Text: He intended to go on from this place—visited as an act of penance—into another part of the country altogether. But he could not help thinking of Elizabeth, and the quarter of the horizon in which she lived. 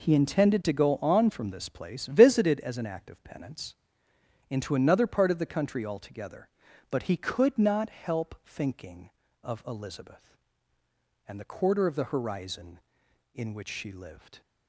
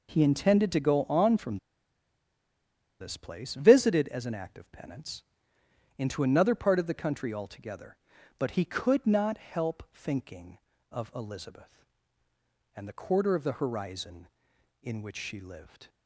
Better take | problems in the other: first | pauses between "from" and "this"; strong; at 1.5 s; 1.4 s long

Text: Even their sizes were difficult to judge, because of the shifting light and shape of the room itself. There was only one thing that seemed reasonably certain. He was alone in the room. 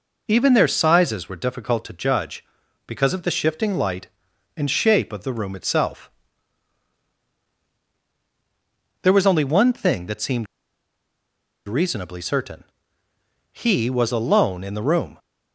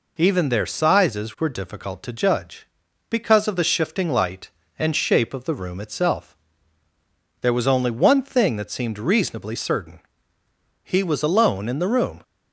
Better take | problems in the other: second | pauses between "seemed" and "reasonably"; at 10.4 s; 1.2 s long

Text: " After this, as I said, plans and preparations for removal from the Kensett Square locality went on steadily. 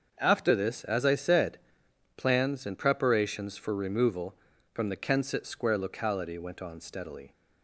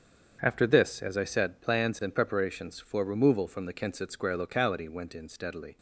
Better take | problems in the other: first | starts louder than the rest; until 1.4 s; 7 dB; also in the first // says "in" for "on"; at 5.1 s

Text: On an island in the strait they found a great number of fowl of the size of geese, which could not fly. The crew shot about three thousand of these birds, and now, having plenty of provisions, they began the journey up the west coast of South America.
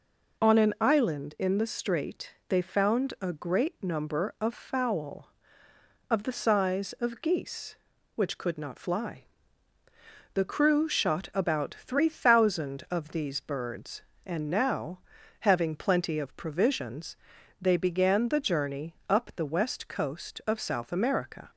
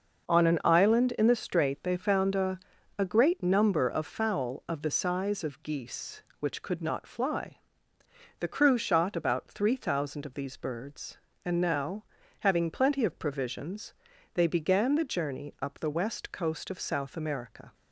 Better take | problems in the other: first | starts louder than the rest; noticeable; until 1.4 s; 6 dB // says "a" twice; at 2.9 s

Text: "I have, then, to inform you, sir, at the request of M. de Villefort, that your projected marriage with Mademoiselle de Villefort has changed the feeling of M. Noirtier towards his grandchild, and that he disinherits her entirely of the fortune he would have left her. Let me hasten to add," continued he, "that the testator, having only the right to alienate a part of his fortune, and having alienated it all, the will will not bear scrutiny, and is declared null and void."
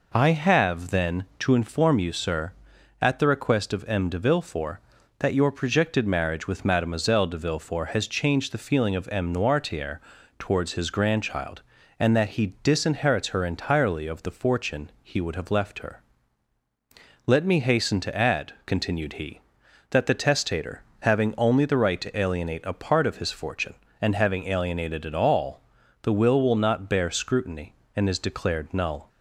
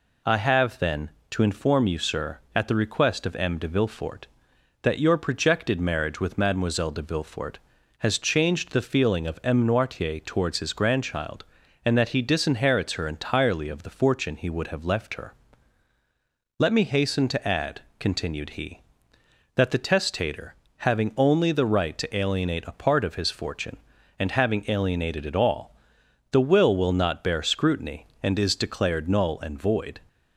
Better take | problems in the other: second | pauses between "Noirtier" and "towards"; at 10.0 s; 0.38 s long // stops before "and void"; at 29.0 s

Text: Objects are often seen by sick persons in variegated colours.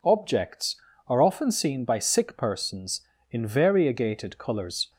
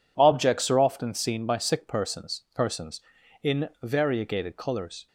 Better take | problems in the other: first | says "persons" twice; at 2.5 s

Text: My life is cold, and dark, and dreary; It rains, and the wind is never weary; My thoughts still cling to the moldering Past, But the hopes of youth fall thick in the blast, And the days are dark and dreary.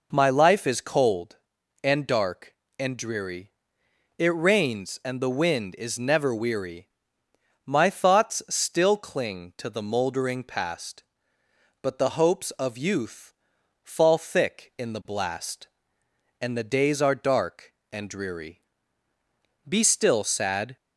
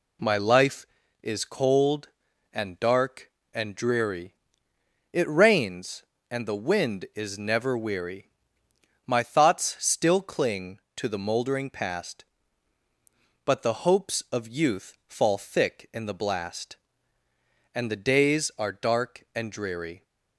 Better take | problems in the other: second | pauses between "youth" and "fall"; noticeable; at 13.3 s; 0.52 s long // goes on to say "Be still sad"; noticeable; from 19.6 s on; 1.0 s long

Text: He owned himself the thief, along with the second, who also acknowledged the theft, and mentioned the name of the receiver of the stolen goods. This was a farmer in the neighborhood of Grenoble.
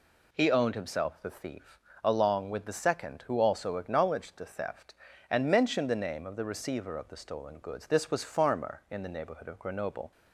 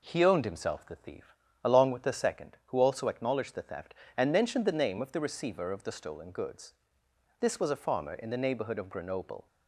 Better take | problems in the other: second | skips "a"; at 8.2 s

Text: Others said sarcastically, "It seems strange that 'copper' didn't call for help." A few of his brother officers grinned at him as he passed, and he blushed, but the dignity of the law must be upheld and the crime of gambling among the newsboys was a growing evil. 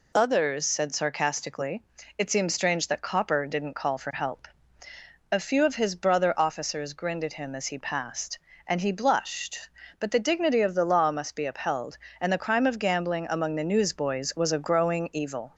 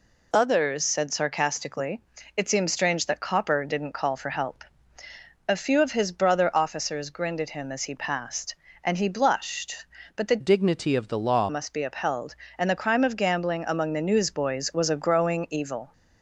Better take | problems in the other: first | changes voice from "dignity" to "law"; from 10.3 to 11.4 s; 1.1 s long

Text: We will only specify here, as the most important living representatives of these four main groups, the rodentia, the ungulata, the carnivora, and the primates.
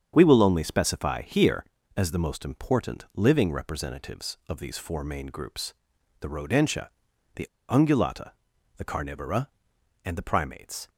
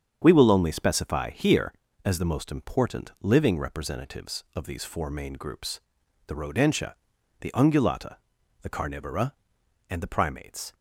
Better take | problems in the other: second | starts louder than the rest; strong; until 1.1 s; 7.5 dB; strong in the second // pauses between "the" and "ungulata"; slight; at 7.4 s; 0.24 s long

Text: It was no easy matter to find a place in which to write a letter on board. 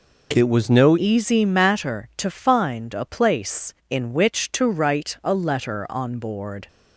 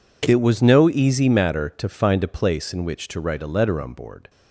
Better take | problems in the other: second | changes voice at "easy"; from 0.9 s on; 5.7 s long

